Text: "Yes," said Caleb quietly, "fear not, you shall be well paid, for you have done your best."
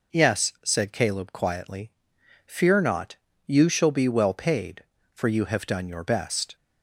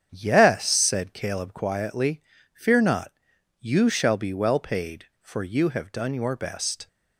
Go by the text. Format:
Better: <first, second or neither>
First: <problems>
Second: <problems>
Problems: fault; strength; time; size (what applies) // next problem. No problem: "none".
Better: first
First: none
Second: starts louder than the rest; strong; until 1.6 s; 8.5 dB